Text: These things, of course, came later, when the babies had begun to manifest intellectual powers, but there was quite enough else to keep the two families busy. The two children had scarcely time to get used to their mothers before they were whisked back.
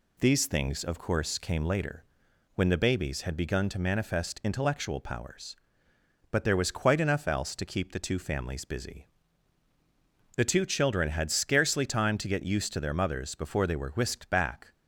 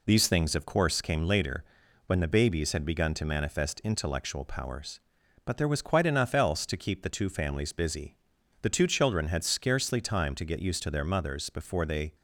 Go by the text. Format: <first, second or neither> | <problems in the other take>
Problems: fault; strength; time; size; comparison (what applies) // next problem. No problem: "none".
first | stops before "were whisked back"; at 12.1 s